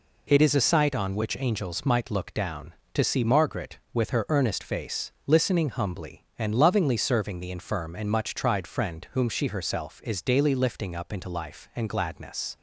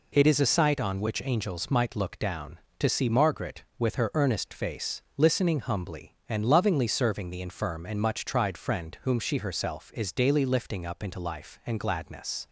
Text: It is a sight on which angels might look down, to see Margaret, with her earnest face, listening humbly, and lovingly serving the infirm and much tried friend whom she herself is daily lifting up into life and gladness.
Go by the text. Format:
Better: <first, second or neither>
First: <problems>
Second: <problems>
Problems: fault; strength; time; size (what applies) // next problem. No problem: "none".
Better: neither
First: none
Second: none